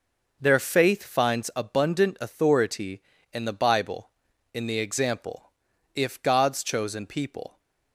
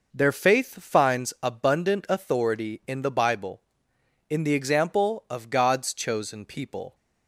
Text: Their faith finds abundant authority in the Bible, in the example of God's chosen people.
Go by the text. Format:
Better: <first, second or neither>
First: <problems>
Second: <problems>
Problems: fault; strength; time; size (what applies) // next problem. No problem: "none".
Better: second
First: says "if" for "of"; at 5.9 s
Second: none